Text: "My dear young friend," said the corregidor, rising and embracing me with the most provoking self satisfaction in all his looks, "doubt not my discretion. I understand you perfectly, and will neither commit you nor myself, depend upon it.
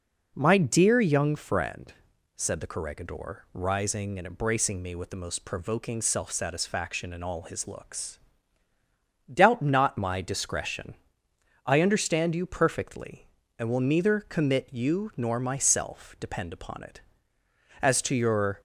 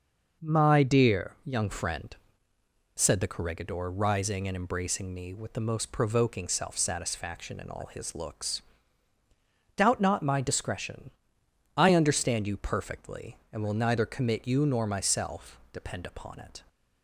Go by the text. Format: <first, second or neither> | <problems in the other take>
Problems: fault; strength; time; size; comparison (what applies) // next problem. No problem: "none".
second | goes on to say "As to your"; noticeable; from 17.8 s on; 0.80 s long